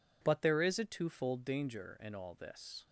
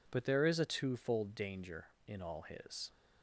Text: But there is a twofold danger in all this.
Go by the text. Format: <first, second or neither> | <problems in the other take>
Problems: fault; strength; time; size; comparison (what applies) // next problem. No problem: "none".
first | says "his" for "this"; at 2.4 s